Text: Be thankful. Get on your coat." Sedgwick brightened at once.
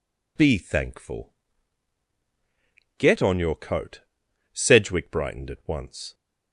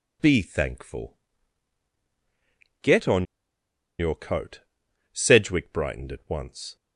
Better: first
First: none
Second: pauses between "on" and "your"; noticeable; at 3.2 s; 0.75 s long

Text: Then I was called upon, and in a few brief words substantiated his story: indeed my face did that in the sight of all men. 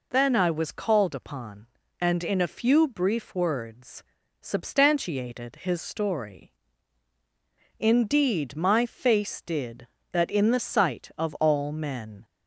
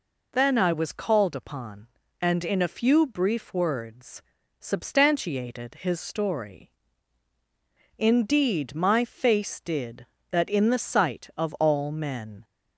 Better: neither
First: pauses between "words" and "substantiated"; at 4.0 s; 0.40 s long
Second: pauses between "words" and "substantiated"; at 4.1 s; 0.40 s long

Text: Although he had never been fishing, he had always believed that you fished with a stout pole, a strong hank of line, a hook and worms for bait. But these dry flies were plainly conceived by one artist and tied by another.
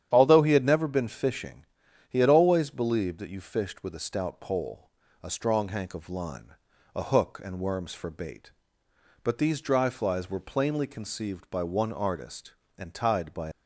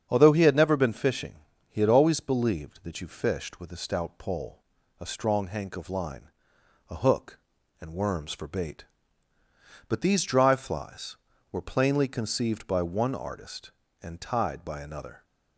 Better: second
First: starts louder than the rest; strong; until 1.1 s; 9.5 dB // stops before "another"; at 13.5 s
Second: starts louder than the rest; strong; until 1.1 s; 7.5 dB

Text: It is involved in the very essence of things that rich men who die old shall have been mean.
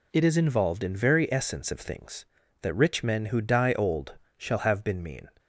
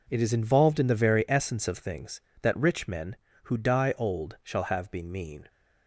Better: second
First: skips "the"; at 0.9 s // pauses between "old" and "shall"; slight; at 4.1 s; 0.22 s long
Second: none

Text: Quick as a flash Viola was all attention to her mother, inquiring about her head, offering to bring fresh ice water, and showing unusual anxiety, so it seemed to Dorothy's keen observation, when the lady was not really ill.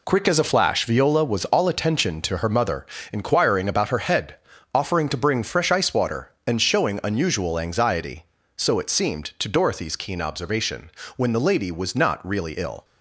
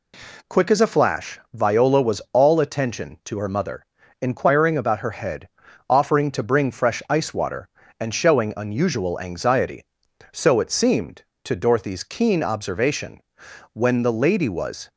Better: first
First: none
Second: stops before "not really ill"; at 14.8 s

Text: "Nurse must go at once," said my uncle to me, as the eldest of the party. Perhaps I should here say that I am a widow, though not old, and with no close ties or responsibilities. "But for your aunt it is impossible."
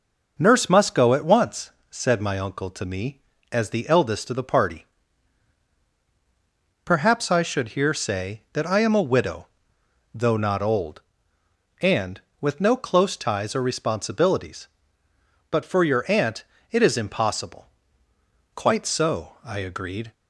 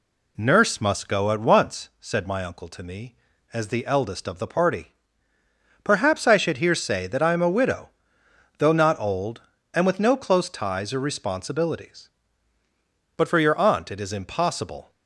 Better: second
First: pauses between "aunt" and "it"; slight; at 16.4 s; 0.26 s long // goes on to say "Quite so I agreed"; from 18.5 s on; 1.5 s long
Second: none

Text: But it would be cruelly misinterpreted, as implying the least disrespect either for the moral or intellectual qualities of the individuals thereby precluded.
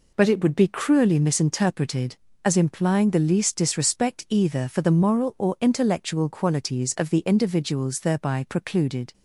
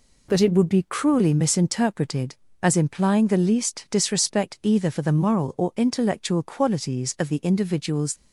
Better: first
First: none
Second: stops before "thereby precluded"; at 8.1 s

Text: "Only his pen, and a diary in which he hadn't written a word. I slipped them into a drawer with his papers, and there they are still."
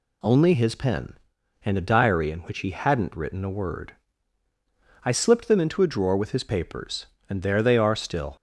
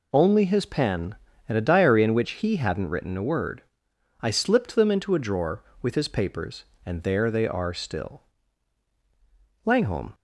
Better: first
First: none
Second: goes on to say "Langholm"; slight; from 9.6 s on; 0.48 s long

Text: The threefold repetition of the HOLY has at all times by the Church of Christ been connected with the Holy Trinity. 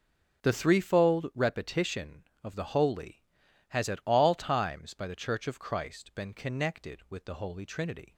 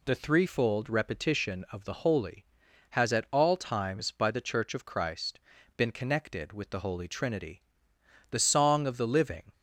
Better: first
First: none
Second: pauses between "Christ" and "been"; at 5.3 s; 0.38 s long // goes on to say "The song of the living"; noticeable; from 8.3 s on; 1.2 s long

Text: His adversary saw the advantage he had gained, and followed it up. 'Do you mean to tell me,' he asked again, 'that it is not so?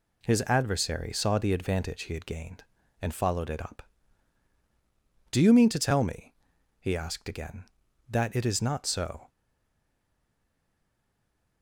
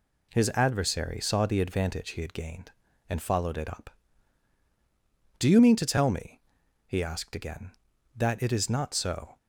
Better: second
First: stays silent after the last word; from 9.2 s on; 2.4 s long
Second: none

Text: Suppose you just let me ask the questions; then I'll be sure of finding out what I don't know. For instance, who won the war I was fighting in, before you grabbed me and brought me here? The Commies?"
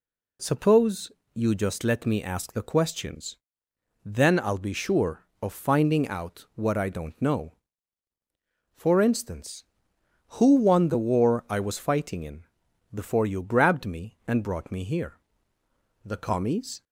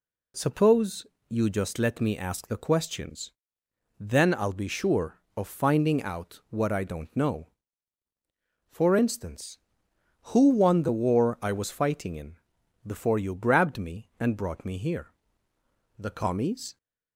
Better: neither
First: pauses between "Suppose" and "you"; slight; at 1.1 s; 0.22 s long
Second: pauses between "Suppose" and "you"; slight; at 1.0 s; 0.22 s long

